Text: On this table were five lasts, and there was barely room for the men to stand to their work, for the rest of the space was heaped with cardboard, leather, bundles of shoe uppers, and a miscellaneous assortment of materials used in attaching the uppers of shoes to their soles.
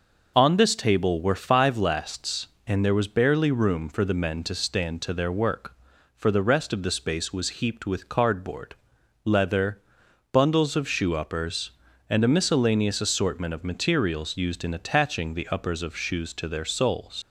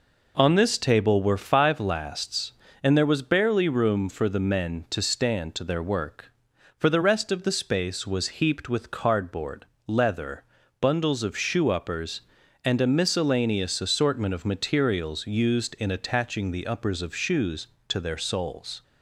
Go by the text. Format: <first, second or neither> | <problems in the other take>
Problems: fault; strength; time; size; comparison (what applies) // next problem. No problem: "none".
second | leaves "soles" unfinished; at 17.2 s; 100 ms